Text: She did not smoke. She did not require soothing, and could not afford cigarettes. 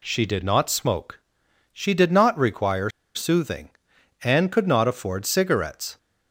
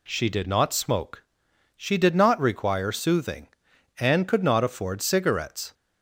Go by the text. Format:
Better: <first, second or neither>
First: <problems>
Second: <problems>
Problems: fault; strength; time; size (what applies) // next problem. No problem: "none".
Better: second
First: pauses between "require" and "soothing"; slight; at 2.8 s; 0.25 s long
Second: none